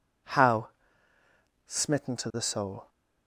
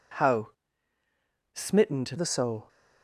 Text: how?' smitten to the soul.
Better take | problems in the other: first | changes voice from "smitten" to "to"; from 1.5 to 2.1 s; 0.6 s long

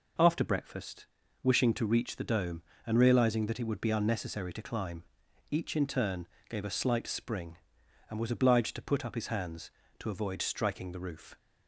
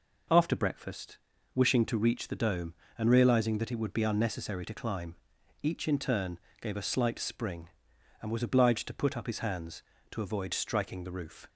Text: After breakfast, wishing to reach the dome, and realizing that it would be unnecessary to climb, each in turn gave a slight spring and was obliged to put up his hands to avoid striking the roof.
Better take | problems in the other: neither | pauses between "turn" and "gave"; slight; the same in both

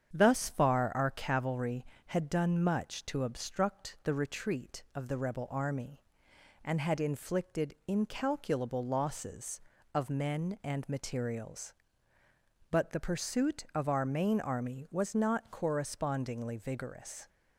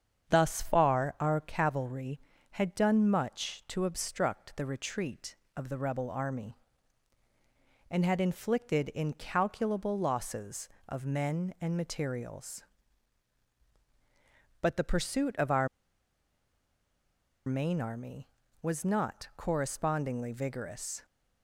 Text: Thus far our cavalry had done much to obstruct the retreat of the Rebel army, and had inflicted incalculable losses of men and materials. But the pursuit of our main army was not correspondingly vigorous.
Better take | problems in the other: first | starts louder than the rest; strong; until 1.3 s; 7.5 dB; strong in the first // pauses between "our" and "main"; strong; at 15.6 s; 1.7 s long

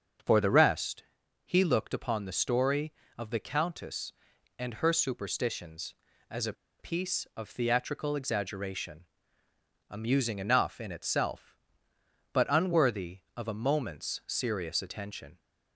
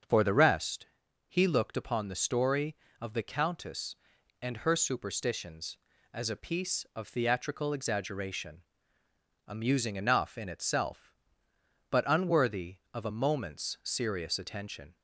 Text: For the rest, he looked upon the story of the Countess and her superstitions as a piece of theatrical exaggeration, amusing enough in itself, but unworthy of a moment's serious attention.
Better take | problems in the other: second | starts louder than the rest; until 1.6 s; 6.5 dB; also in the second // pauses between "a" and "piece"; slight; at 6.5 s; 0.26 s long

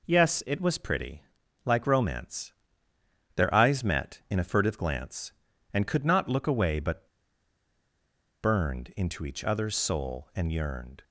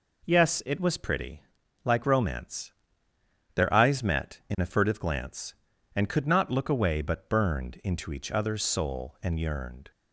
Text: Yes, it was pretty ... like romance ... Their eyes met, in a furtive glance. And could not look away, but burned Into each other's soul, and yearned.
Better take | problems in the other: second | pauses between "but" and "burned"; strong; at 7.0 s; 1.3 s long

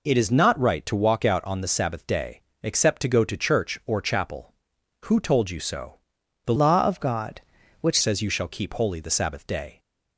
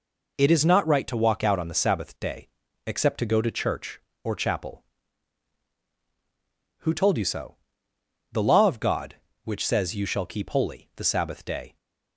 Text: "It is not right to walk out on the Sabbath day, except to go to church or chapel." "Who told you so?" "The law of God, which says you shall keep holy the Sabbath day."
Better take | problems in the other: second | changes voice from "law" to "which"; from 6.5 to 7.9 s; 1.4 s long

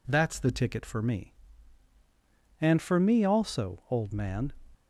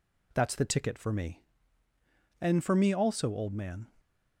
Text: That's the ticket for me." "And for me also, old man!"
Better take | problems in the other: neither | none

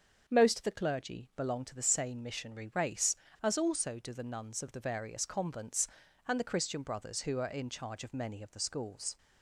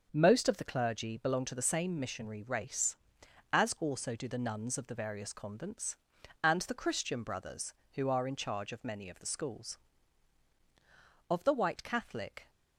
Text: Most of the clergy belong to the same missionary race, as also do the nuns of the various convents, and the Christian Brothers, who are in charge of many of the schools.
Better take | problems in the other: first | starts louder than the rest; until 1.1 s; 6.5 dB; also in the first // goes on to say "Of the white Catholic"; noticeable; from 11.2 s on; 1.2 s long

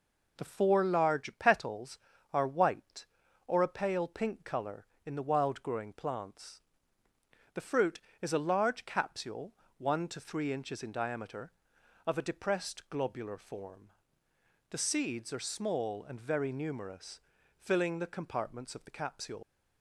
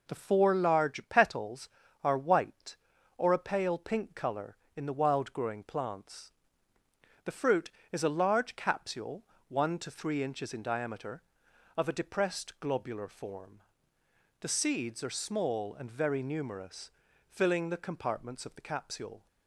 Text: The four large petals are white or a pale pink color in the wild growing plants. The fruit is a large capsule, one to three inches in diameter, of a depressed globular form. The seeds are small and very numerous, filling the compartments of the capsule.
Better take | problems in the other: second | leaves "capsule" unfinished; at 19.4 s; 130 ms

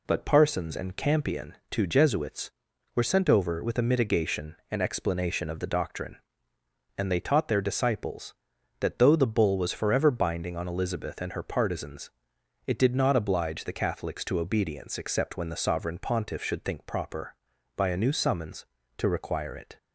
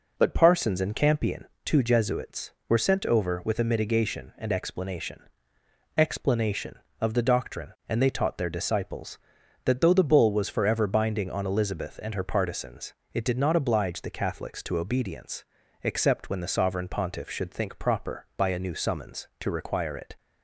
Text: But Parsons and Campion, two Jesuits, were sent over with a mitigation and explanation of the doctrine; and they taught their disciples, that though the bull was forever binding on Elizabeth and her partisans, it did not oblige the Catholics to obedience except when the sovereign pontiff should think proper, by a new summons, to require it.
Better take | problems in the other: first | says "explanation" twice; at 5.9 s // pauses between "obedience" and "except"; at 15.4 s; 0.38 s long

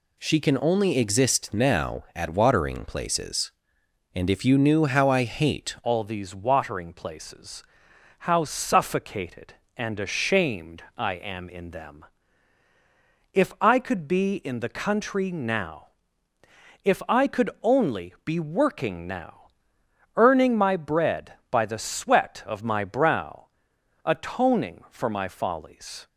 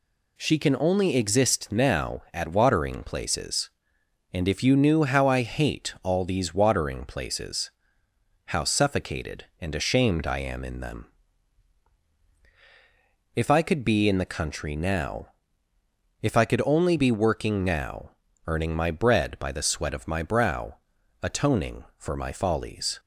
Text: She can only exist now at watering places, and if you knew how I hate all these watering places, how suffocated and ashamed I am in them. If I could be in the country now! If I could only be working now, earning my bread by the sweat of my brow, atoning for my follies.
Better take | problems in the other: second | changes voice at "all"; from 5.8 s on; 20.2 s long

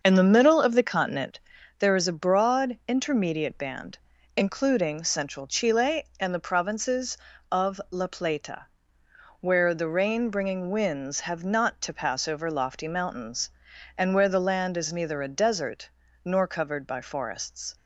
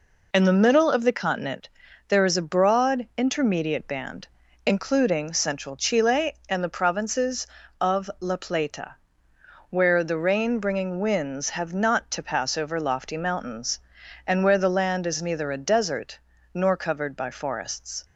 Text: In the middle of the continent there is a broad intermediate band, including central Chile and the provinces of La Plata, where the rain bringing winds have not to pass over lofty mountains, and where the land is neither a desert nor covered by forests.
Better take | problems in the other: second | starts louder than the rest; until 1.8 s; 6.5 dB // pauses between "continent" and "there"; at 1.3 s; 0.40 s long; also in the second // pauses between "desert" and "nor"; at 15.8 s; 0.38 s long; also in the second

